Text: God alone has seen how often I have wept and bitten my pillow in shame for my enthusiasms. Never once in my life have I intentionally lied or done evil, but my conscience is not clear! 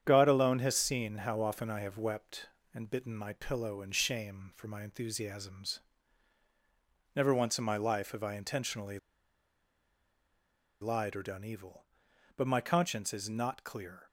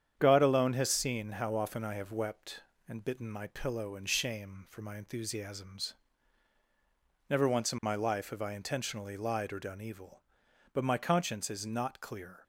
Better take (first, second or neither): second